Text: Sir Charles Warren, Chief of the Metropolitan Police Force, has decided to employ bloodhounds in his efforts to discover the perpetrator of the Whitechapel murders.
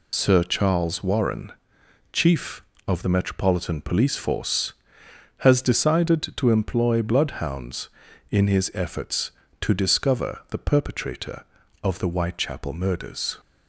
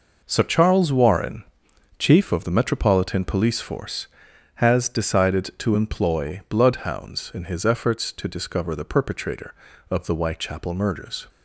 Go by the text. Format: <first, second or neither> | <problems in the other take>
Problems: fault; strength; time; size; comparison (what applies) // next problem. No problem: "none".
second | loses the start of "Sir"; at 0.1 s; 80 ms